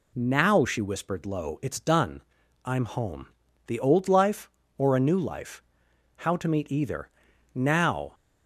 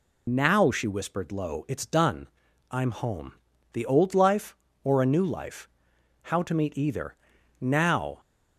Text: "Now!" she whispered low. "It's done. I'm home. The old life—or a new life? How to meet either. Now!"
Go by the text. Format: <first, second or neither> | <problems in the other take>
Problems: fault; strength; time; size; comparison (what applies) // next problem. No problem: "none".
first | loses the start of "Now"; at 0.2 s; 65 ms